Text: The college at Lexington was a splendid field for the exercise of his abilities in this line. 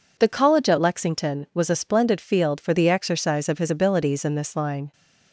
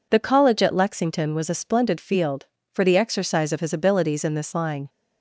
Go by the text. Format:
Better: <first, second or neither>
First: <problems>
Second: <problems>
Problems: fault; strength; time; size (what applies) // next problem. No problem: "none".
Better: neither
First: none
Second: none